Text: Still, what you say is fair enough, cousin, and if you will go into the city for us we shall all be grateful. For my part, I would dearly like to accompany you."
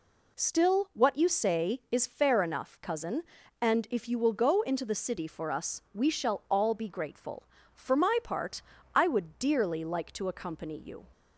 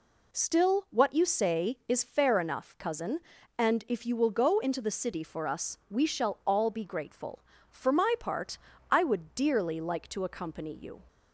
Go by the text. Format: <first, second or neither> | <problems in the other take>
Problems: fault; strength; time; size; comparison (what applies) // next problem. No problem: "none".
neither | none